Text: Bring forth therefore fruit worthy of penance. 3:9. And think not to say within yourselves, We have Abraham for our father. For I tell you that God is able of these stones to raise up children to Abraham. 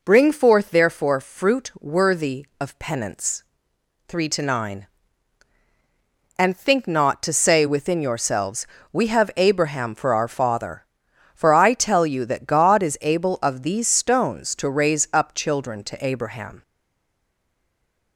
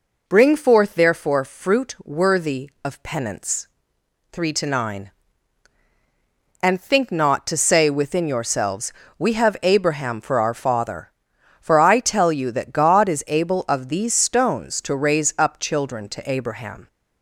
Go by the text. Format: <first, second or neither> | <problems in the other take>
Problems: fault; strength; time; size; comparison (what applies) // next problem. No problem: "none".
second | stays silent after the last word; noticeable; from 16.6 s on; 1.5 s long